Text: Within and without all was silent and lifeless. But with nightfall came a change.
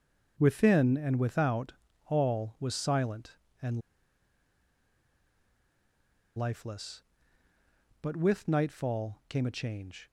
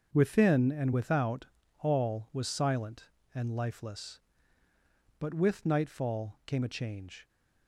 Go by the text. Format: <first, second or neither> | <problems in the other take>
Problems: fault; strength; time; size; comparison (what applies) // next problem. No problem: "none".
second | starts louder than the rest; until 1.4 s; 6.5 dB; also in the second // pauses between "without" and "all"; slight; at 1.7 s; 0.34 s long; slight in the second // pauses between "and" and "lifeless"; strong; at 3.8 s; 2.5 s long